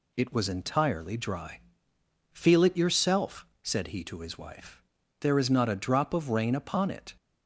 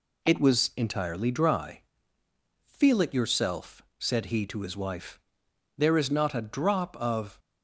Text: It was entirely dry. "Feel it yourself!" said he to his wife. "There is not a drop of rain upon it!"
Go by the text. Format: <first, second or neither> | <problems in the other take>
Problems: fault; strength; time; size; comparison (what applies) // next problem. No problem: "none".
first | stops before "rain upon it"; at 7.3 s